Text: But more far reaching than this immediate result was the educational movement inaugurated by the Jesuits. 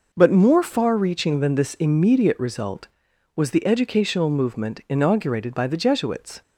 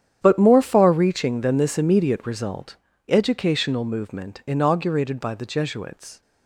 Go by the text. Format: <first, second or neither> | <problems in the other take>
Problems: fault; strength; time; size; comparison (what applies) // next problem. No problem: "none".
first | starts louder than the rest; strong; until 1.2 s; 9.5 dB // skips "was the"; at 2.9 s